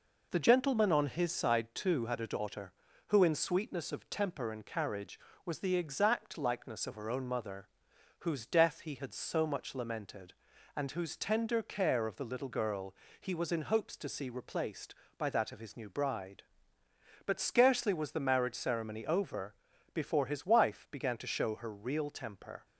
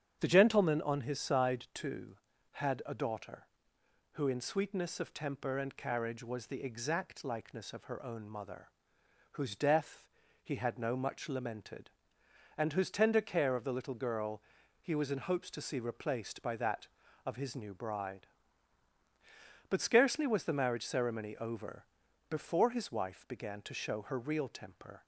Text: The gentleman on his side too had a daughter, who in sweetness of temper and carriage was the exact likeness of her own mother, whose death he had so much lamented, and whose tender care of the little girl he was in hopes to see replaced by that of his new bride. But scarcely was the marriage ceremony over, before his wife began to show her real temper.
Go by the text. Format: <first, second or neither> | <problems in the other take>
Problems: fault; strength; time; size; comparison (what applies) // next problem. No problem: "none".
first | starts louder than the rest; strong; until 1.2 s; 8.5 dB // pauses between "death" and "he"; at 10.0 s; 0.40 s long // says "no" for "so"; at 10.7 s // pauses between "girl" and "he"; at 14.4 s; 0.40 s long; slight in the first